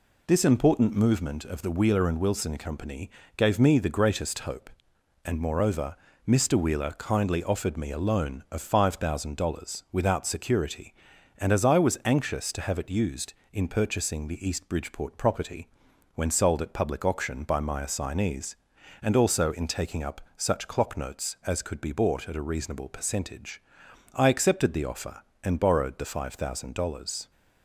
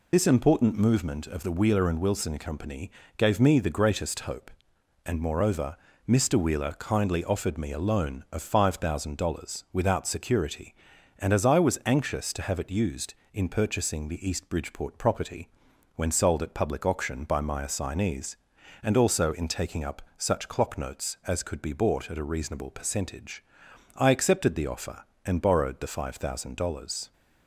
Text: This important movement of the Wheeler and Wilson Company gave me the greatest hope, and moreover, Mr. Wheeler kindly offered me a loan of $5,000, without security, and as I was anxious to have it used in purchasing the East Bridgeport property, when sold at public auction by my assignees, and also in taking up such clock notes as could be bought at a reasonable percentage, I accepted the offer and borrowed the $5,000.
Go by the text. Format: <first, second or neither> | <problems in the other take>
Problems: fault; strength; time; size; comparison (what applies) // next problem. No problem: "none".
first | loses the start of "This"; at 0.1 s; 35 ms // pauses between "Company" and "gave"; slight; at 2.9 s; 0.28 s long; slight in the first // pauses between "up" and "such"; slight; at 20.0 s; 0.16 s long; slight in the first